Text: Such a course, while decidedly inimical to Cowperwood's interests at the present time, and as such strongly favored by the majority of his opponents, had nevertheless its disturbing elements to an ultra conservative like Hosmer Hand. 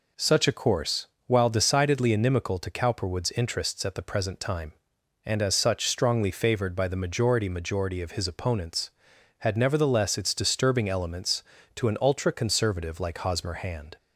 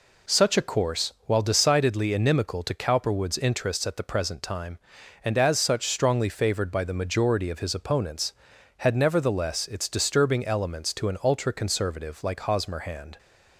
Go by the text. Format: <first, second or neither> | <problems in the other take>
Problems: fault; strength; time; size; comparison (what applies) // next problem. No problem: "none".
second | says "majority" twice; at 7.4 s